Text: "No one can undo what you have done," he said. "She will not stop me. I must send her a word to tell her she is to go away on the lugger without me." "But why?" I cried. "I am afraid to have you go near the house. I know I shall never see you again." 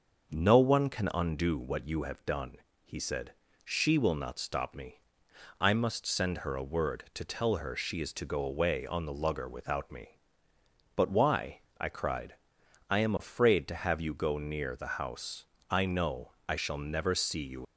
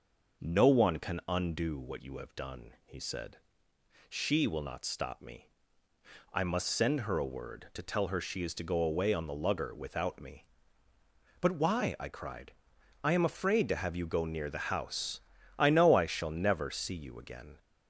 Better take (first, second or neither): second